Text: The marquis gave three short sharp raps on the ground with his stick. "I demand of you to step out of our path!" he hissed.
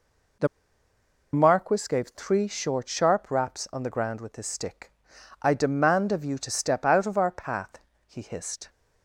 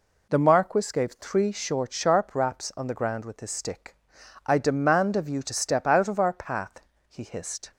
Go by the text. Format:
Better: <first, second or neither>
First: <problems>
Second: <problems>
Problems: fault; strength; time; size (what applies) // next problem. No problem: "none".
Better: second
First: pauses between "The" and "marquis"; noticeable; at 0.4 s; 0.86 s long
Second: none